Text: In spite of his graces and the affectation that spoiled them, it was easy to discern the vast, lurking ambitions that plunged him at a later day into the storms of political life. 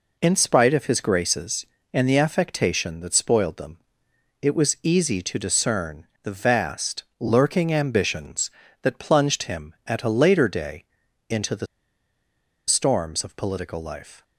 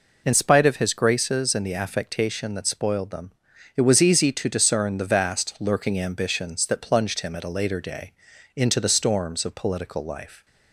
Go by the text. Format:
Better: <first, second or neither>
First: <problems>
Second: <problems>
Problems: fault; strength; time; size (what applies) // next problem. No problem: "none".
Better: second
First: pauses between "discern" and "the"; slight; at 6.0 s; 0.16 s long // pauses between "day" and "into"; at 10.8 s; 0.44 s long // pauses between "the" and "storms"; at 11.6 s; 1.0 s long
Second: pauses between "day" and "into"; at 8.1 s; 0.44 s long